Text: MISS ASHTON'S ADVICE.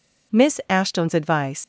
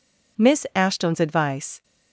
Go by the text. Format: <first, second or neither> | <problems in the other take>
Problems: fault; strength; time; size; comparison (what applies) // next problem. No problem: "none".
second | leaves "ADVICE" unfinished; at 1.6 s; 130 ms